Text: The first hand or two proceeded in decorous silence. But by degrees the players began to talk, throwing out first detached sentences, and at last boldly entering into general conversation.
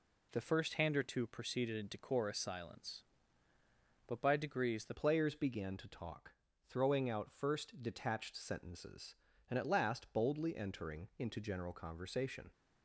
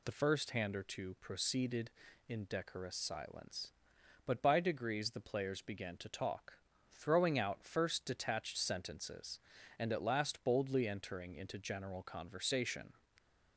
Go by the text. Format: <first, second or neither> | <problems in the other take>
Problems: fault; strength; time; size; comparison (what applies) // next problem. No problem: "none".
second | changes voice at "players"; from 4.9 s on; 7.6 s long